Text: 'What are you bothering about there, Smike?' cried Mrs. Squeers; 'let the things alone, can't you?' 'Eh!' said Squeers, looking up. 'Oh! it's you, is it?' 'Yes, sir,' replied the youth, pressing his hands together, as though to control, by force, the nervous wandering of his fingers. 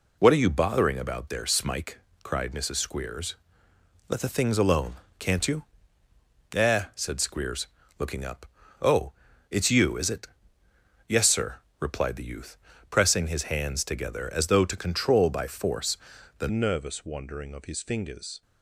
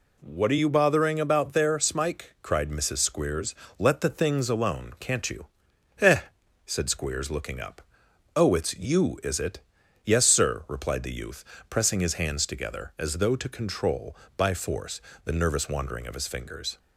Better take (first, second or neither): second